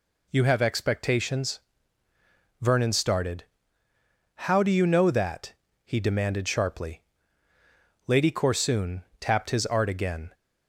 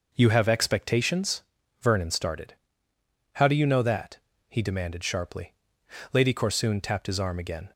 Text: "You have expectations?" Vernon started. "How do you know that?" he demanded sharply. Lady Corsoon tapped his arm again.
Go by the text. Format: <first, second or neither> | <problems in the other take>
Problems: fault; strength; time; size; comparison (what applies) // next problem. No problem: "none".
second | pauses between "Corsoon" and "tapped"; slight; at 9.0 s; 0.16 s long // says "art" for "arm"; at 9.6 s